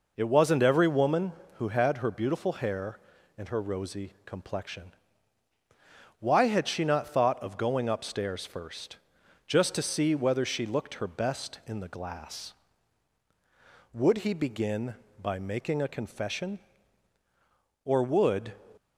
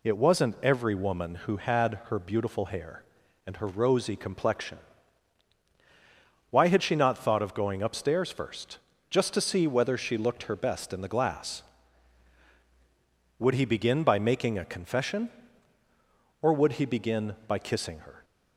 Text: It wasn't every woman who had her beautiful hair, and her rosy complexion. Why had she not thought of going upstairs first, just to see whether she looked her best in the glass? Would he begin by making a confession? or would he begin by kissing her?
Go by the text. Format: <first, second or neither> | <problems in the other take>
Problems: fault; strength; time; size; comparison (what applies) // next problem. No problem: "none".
second | stops before "he begin by kissing her"; at 18.7 s